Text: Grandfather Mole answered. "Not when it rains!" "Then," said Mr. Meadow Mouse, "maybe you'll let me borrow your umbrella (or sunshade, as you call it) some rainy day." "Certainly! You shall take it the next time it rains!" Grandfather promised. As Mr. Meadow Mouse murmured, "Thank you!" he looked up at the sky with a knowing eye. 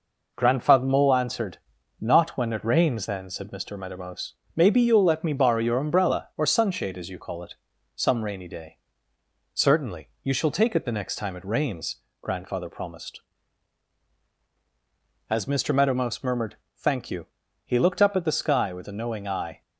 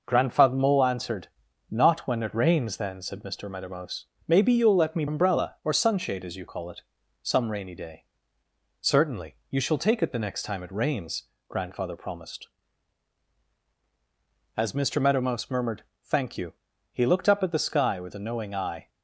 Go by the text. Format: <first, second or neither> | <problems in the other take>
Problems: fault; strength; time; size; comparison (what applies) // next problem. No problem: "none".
first | skips "borrow your"; at 5.0 s